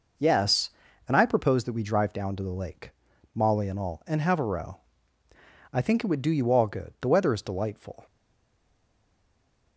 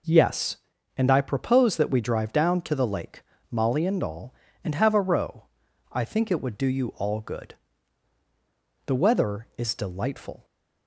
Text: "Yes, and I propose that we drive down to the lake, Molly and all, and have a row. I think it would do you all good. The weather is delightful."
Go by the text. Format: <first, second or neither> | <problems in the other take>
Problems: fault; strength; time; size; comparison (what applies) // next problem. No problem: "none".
second | stays silent after the last word; noticeable; from 8.0 s on; 1.7 s long